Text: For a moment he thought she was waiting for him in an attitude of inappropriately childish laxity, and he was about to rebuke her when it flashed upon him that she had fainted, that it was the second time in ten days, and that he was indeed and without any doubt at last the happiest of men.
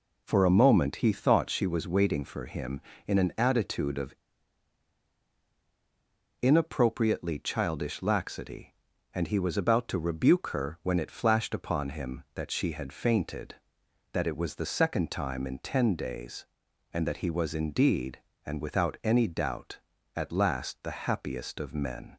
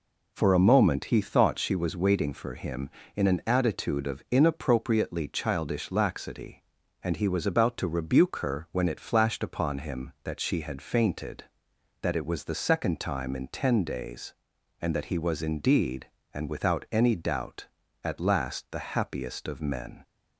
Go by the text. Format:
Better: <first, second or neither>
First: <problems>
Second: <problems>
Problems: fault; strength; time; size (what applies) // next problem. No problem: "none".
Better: second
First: pauses between "of" and "inappropriately"; strong; at 4.1 s; 2.2 s long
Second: none